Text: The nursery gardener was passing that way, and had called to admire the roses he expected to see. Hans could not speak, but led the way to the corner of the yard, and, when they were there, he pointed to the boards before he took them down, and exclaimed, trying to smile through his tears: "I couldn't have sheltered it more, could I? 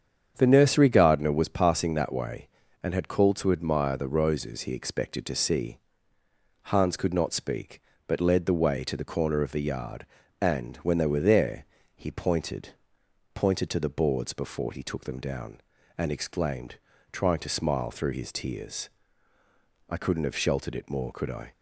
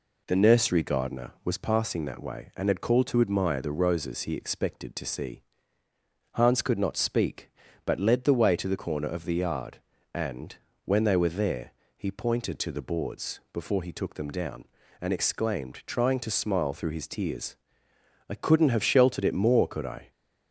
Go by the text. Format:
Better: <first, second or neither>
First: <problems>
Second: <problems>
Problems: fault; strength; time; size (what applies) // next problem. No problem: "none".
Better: second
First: starts louder than the rest; strong; until 1.3 s; 8 dB // says "pointed" twice; at 13.3 s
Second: none